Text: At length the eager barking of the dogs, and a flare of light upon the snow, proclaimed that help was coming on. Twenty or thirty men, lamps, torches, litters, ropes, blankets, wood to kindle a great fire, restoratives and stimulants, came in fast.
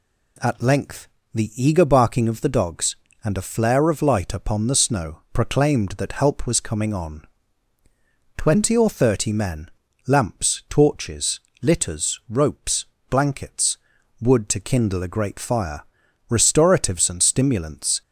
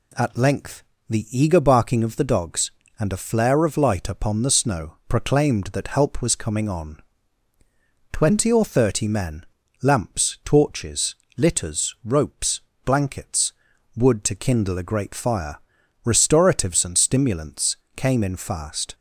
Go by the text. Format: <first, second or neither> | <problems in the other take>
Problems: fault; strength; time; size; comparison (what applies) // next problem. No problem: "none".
second | pauses between "length" and "the"; slight; at 1.0 s; 0.26 s long; slight in the second // stops before "came in fast"; at 18.0 s